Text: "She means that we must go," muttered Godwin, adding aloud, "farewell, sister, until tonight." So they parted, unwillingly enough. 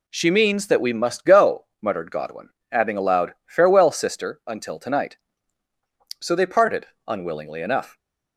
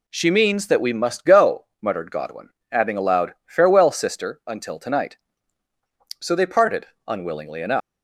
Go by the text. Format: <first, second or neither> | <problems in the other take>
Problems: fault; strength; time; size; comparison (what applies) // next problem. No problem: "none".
first | leaves "enough" unfinished; at 7.8 s; 185 ms